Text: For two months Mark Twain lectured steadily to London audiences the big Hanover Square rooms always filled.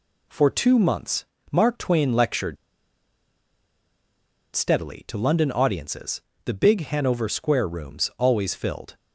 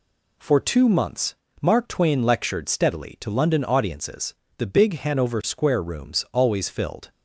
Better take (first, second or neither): second